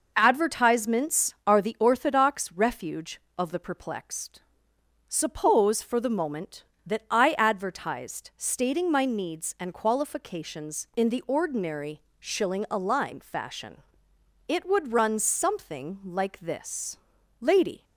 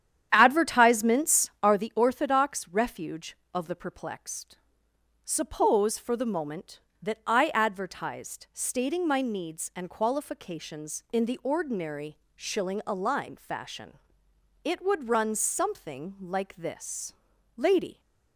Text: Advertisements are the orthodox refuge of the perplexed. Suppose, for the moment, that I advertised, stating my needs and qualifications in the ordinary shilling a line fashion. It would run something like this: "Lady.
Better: first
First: pauses between "ordinary" and "shilling"; slight; at 11.9 s; 0.20 s long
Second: starts louder than the rest; strong; until 1.8 s; 9.5 dB // pauses between "ordinary" and "shilling"; slight; at 12.1 s; 0.20 s long

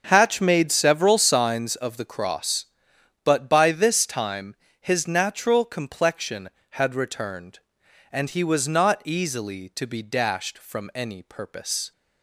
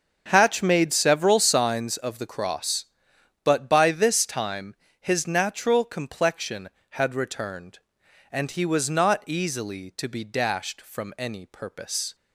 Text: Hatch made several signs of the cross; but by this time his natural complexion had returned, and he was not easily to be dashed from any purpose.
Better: neither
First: starts louder than the rest; until 1.1 s; 7 dB // pauses between "time" and "his"; slight; at 4.5 s; 0.24 s long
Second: starts louder than the rest; until 1.3 s; 7 dB // pauses between "time" and "his"; slight; at 4.7 s; 0.24 s long

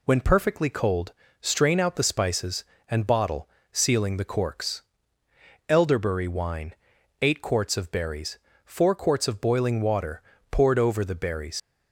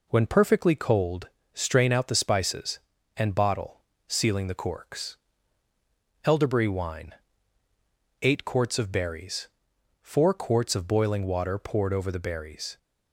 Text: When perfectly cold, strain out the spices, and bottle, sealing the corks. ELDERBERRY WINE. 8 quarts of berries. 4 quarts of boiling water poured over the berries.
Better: second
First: pauses between "water" and "poured"; slight; at 10.2 s; 0.30 s long // leaves "berries" unfinished; at 11.5 s; 110 ms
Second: none

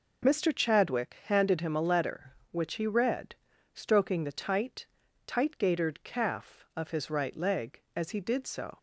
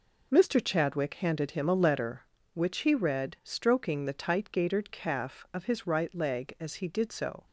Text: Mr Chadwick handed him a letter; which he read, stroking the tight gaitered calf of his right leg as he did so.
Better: second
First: says "tight" twice; at 5.2 s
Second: none

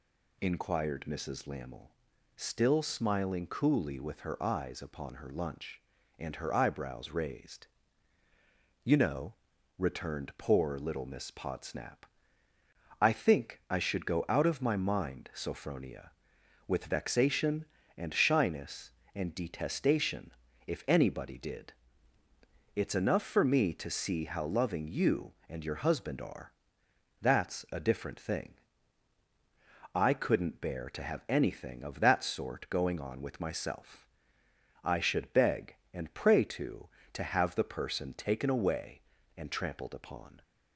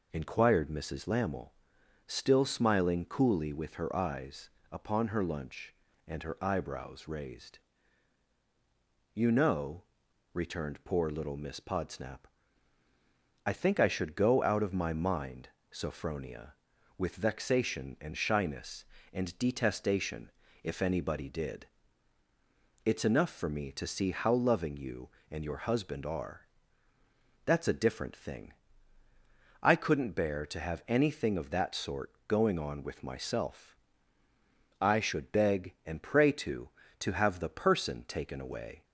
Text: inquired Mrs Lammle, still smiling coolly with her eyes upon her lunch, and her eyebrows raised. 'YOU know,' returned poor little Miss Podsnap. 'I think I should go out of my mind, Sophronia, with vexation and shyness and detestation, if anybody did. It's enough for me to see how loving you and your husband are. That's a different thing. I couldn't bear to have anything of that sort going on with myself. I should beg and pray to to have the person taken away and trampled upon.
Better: first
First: none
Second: pauses between "eyes" and "upon"; slight; at 4.5 s; 0.22 s long // pauses between "sort" and "going"; slight; at 32.1 s; 0.16 s long // stops before "and trampled upon"; at 38.8 s

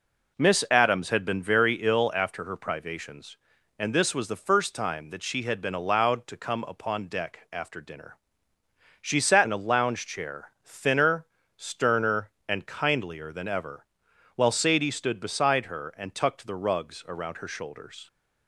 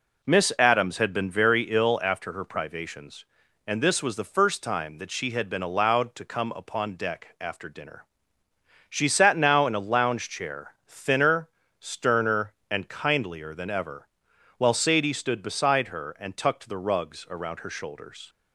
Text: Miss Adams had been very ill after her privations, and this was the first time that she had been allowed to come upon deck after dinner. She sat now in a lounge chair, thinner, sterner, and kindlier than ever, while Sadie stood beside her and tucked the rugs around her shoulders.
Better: second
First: skips "now"; at 9.4 s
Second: none

